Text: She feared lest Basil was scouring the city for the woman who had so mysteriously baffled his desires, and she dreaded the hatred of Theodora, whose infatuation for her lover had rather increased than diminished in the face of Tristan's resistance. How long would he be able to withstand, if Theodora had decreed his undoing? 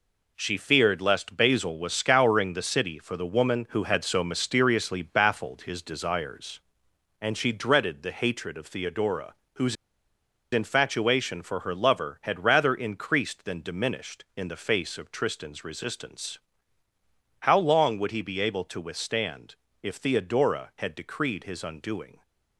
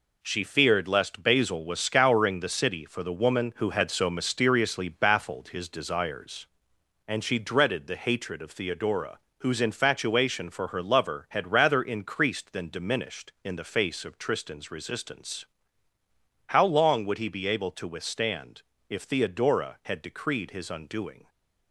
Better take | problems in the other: second | pauses between "whose" and "infatuation"; noticeable; at 9.7 s; 0.78 s long

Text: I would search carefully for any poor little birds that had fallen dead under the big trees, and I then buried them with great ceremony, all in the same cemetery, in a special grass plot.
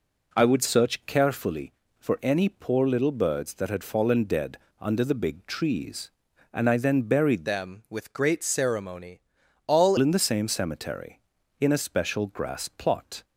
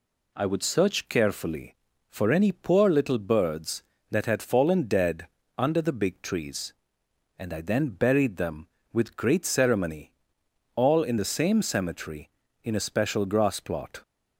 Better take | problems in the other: second | pauses between "dead" and "under"; slight; at 4.5 s; 0.24 s long; slight in the second // changes voice from "them" to "all"; from 7.4 to 9.9 s; 2.5 s long

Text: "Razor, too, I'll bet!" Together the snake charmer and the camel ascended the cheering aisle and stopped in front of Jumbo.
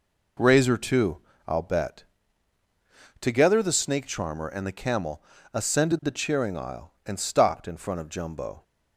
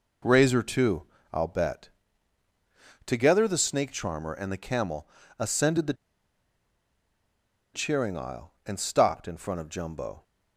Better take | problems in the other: first | pauses between "camel" and "ascended"; slight; at 5.0 s; 0.32 s long; slight in the first // pauses between "the" and "cheering"; strong; at 5.9 s; 1.8 s long

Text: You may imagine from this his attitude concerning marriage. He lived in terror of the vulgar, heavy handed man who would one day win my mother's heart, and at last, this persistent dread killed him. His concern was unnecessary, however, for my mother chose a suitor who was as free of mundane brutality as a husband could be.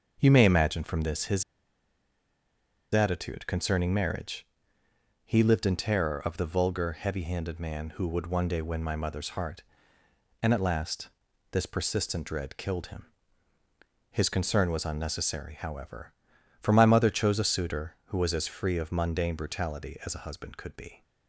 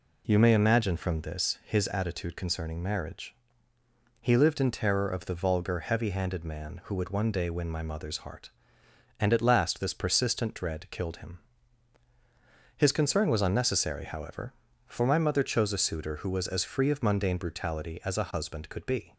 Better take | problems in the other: second | starts louder than the rest; until 1.2 s; 6.5 dB // pauses between "his" and "attitude"; strong; at 1.4 s; 1.5 s long

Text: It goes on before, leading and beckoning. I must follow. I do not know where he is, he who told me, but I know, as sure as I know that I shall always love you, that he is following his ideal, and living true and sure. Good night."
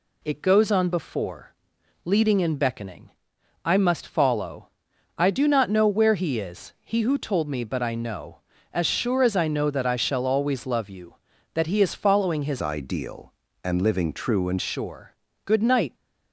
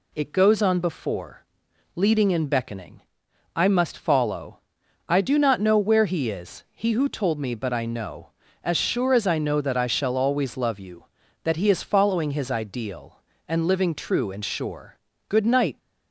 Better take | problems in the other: second | changes voice from "ideal" to "and"; from 12.6 to 14.5 s; 1.9 s long

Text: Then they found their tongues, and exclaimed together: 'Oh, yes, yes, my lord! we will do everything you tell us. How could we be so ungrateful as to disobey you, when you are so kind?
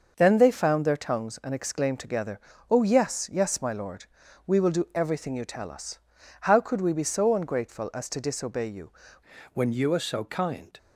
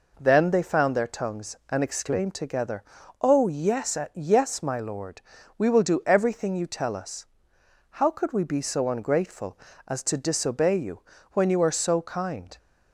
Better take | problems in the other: second | changes voice at "when"; from 9.5 s on; 1.2 s long

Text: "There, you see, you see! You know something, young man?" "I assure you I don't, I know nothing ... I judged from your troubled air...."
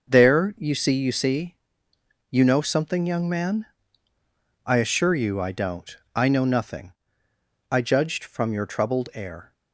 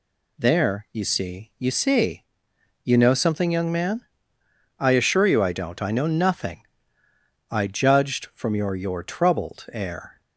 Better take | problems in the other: first | says "your" twice; at 8.7 s

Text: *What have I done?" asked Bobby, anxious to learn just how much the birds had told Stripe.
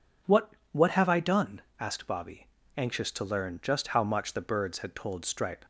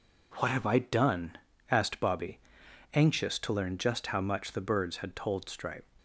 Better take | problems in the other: second | says "What" twice; at 0.7 s

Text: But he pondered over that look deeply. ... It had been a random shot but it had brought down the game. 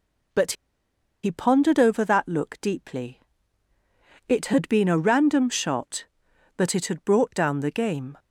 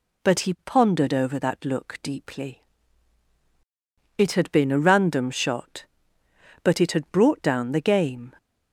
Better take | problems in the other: second | pauses between "But" and "he"; noticeable; at 0.5 s; 0.70 s long

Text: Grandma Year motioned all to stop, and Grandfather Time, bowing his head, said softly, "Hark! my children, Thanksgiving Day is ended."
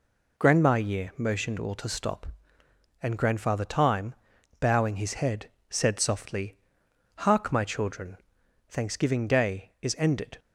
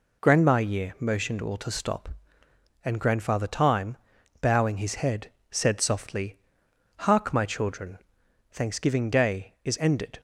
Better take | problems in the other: neither | none

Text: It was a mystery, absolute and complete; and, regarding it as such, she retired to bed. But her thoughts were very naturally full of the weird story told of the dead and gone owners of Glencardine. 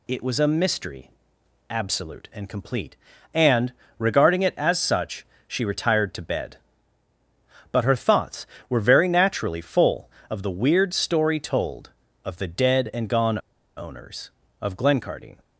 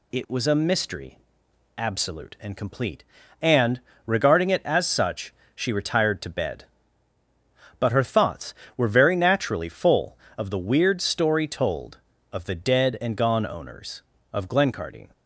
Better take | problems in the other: second | pauses between "gone" and "owners"; at 13.3 s; 0.38 s long

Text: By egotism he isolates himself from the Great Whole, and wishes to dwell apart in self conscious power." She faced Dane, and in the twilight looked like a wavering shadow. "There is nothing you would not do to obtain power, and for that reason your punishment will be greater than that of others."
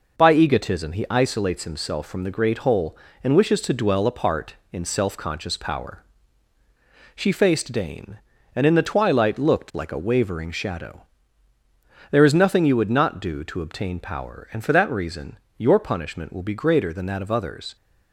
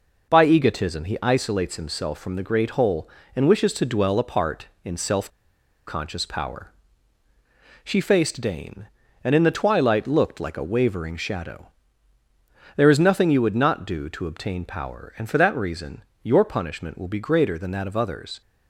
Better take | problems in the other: first | pauses between "self" and "conscious"; noticeable; at 5.2 s; 0.58 s long // pauses between "reason" and "your"; slight; at 16.0 s; 0.22 s long; slight in the first

